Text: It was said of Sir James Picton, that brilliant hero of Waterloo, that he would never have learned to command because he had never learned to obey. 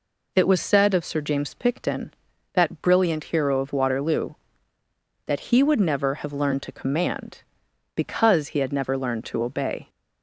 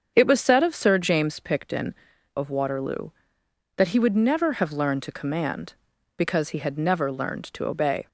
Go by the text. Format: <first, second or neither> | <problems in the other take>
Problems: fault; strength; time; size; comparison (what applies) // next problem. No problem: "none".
first | starts louder than the rest; until 1.1 s; 7 dB // skips "that brilliant hero"; at 2.1 s